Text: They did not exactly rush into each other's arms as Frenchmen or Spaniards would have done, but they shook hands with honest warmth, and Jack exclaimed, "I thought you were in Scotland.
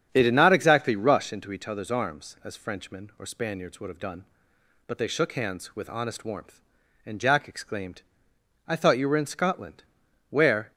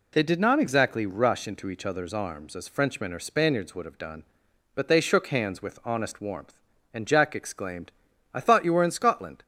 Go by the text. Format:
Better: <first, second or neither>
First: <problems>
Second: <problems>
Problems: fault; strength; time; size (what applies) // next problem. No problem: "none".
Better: second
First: starts louder than the rest; strong; until 1.1 s; 8 dB // goes on to say "Where"; slight; from 10.3 s on; 0.40 s long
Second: none